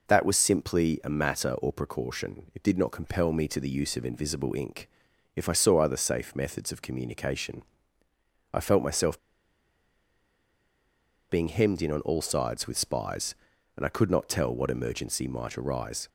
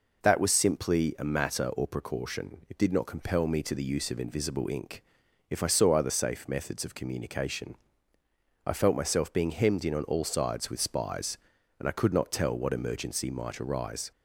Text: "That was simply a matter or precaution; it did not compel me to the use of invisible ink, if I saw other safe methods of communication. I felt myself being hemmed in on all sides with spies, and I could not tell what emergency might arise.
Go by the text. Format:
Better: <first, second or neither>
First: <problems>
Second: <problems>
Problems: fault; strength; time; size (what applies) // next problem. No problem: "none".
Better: second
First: pauses between "myself" and "being"; strong; at 9.1 s; 2.1 s long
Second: none